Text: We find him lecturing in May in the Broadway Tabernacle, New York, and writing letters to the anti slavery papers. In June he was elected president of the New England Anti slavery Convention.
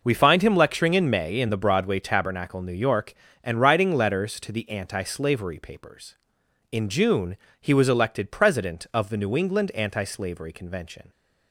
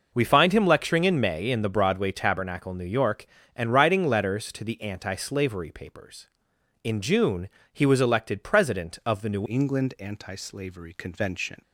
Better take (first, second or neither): first